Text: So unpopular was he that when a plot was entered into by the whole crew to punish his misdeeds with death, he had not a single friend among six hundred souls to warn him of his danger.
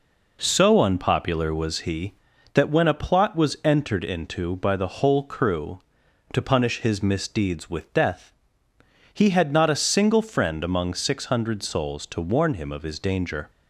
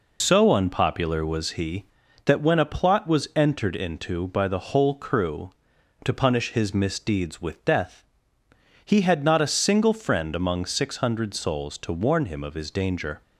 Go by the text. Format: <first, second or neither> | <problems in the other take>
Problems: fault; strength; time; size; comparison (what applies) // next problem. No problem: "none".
first | loses the start of "So"; at 0.2 s; 100 ms